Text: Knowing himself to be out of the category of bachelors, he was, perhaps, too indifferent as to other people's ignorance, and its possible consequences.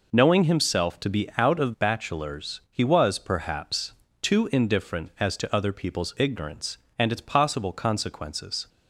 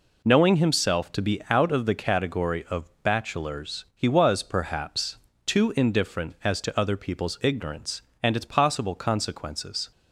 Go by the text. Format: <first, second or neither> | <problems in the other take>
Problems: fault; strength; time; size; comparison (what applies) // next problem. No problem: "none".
second | skips "the category of"; at 1.7 s